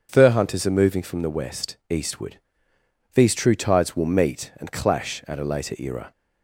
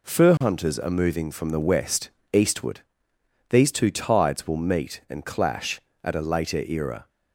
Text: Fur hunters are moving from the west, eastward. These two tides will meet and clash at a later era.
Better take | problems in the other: second | starts louder than the rest; until 1.1 s; 7 dB // says "true" for "two"; at 3.3 s

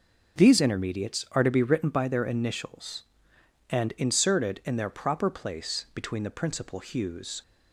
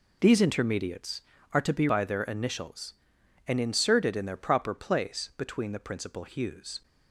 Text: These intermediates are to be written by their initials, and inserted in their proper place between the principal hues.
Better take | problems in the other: first | skips "written"; at 1.8 s

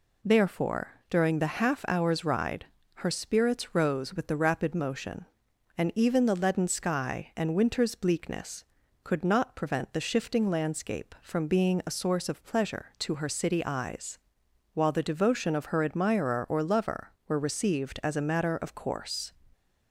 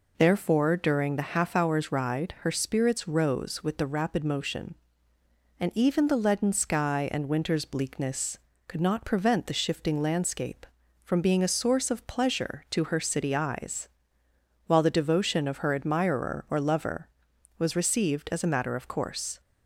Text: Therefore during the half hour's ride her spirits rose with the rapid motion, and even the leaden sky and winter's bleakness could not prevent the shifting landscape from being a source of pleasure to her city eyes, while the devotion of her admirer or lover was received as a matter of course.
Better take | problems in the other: second | pauses between "ride" and "her"; slight; at 2.6 s; 0.30 s long // says "were" for "was"; at 17.2 s

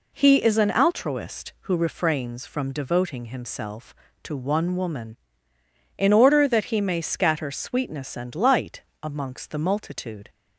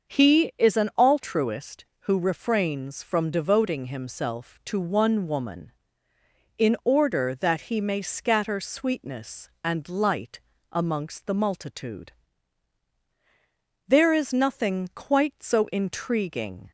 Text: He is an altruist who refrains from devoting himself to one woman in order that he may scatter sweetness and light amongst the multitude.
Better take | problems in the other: first | starts louder than the rest; until 1.2 s; 6.5 dB // pauses between "light" and "amongst"; slight; at 10.4 s; 0.30 s long; slight in the first // goes on to say "There is nothing quite so intriguing"; strong; from 13.8 s on; 2.8 s long

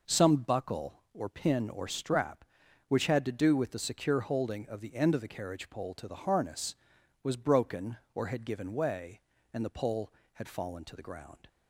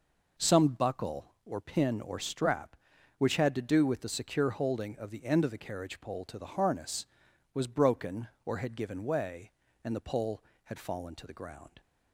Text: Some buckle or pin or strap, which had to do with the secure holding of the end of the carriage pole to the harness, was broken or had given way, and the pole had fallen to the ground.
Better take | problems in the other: neither | none

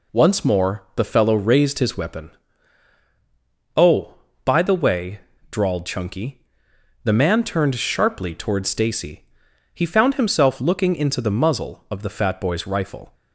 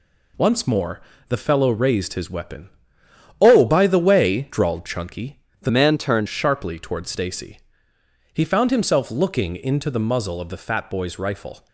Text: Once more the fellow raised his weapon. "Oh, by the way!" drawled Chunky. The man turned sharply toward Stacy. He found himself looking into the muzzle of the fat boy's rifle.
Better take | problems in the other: first | pauses between "more" and "the"; slight; at 1.0 s; 0.28 s long // changes voice from "man" to "turned"; from 5.6 to 6.2 s; 0.6 s long

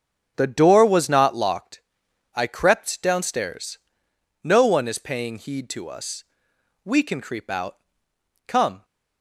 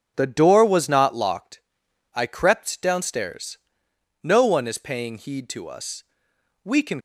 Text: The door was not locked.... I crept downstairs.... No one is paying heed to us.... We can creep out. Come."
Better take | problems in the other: first | starts louder than the rest; strong; until 1.1 s; 7.5 dB; strong in the first // stops before "creep out Come"; at 6.9 s

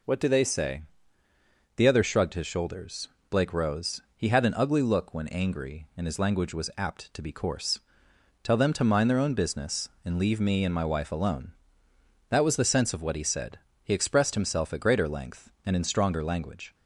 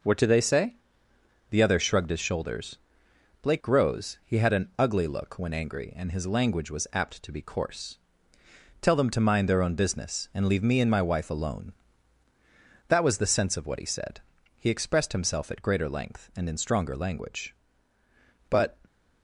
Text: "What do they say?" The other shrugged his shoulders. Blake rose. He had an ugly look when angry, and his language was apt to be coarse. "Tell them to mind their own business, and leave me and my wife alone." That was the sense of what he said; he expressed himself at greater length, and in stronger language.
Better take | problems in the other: first | goes on to say "But"; slight; from 18.4 s on; 0.28 s long

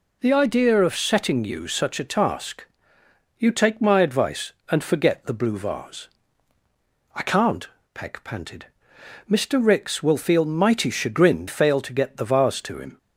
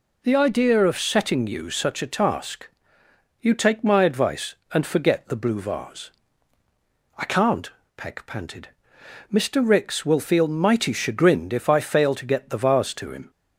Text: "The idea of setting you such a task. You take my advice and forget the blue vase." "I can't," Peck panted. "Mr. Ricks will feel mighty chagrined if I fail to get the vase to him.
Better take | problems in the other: second | skips "if I"; at 11.4 s

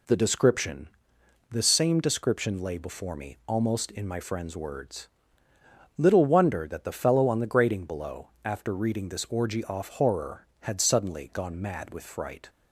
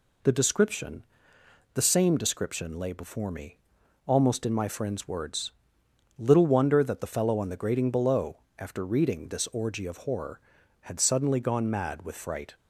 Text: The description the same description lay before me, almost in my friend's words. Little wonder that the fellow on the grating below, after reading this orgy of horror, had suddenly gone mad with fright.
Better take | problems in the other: second | pauses between "description" and "the"; noticeable; at 0.8 s; 0.62 s long; noticeable in the second // says "off" for "of"; at 9.6 s

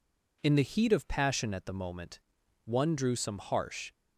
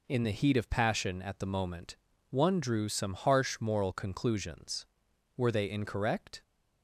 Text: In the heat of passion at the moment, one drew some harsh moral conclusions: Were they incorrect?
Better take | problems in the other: second | stops before "moral conclusions Were they incorrect"; at 3.9 s

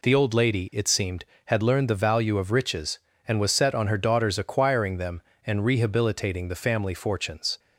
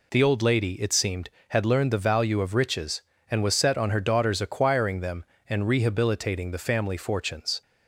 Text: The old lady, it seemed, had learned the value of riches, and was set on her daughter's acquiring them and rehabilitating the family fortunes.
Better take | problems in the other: neither | none

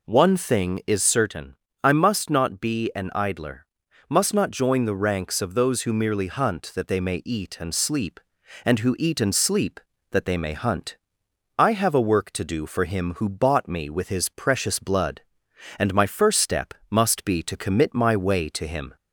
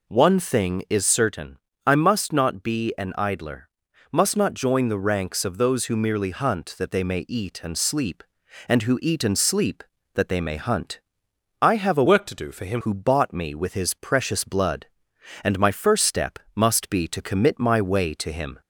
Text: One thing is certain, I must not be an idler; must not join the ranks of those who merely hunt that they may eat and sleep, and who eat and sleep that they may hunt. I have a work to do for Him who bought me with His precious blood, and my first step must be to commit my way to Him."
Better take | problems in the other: first | changes voice from "work" to "Him"; from 12.0 to 12.8 s; 0.8 s long // pauses between "step" and "must"; slight; at 16.3 s; 0.16 s long; slight in the first

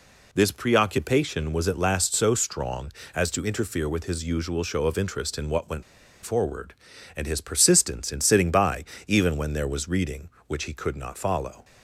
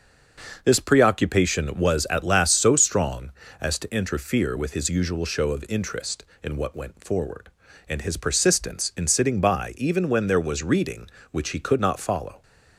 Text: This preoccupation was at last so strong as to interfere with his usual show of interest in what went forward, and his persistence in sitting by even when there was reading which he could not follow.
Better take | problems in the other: second | pauses between "went" and "forward"; at 5.8 s; 0.41 s long // pauses between "by" and "even"; slight; at 8.8 s; 0.22 s long

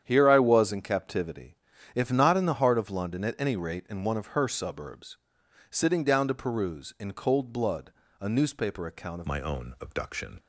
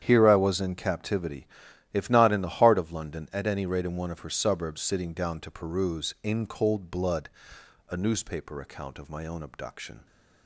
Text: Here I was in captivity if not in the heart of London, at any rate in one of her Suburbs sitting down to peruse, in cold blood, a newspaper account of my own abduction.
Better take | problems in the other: second | starts louder than the rest; strong; until 1.0 s; 9 dB; strong in the second // pauses between "captivity" and "if"; at 1.5 s; 0.40 s long; noticeable in the second // pauses between "Suburbs" and "sitting"; noticeable; at 5.1 s; 0.54 s long // changes voice at "my"; from 9.2 s on; 1.1 s long

